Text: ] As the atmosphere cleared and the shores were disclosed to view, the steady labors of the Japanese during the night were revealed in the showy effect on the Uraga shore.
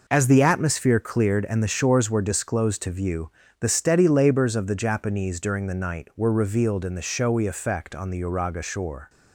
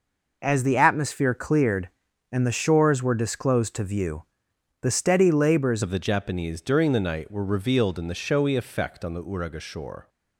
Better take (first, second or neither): first